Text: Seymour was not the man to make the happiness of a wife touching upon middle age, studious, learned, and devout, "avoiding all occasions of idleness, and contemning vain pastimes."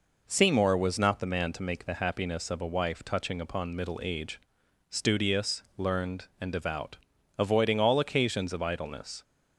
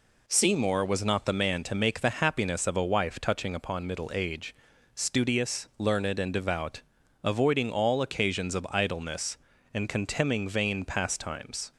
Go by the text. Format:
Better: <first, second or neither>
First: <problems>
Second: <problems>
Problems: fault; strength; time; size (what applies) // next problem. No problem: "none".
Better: second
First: stops before "and contemning vain pastimes"; at 9.2 s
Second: none